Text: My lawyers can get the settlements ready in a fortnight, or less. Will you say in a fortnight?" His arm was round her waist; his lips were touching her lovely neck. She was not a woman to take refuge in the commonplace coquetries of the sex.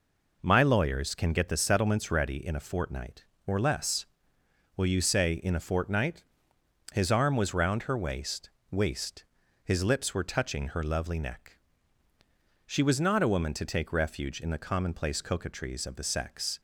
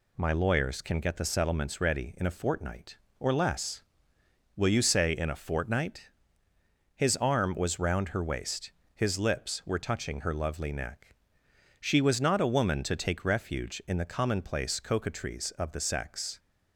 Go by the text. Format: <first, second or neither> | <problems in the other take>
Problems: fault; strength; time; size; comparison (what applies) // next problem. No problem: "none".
second | says "waist" twice; at 8.6 s